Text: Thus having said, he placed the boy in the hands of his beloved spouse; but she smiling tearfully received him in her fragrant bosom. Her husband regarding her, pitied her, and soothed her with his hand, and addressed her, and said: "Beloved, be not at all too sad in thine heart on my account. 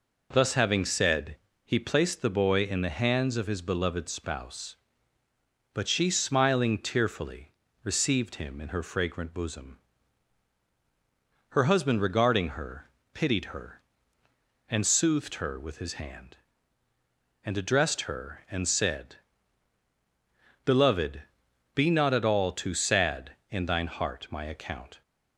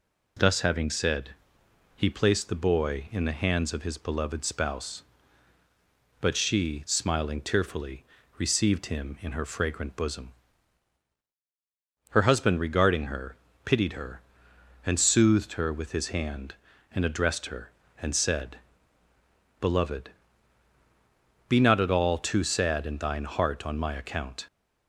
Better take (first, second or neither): second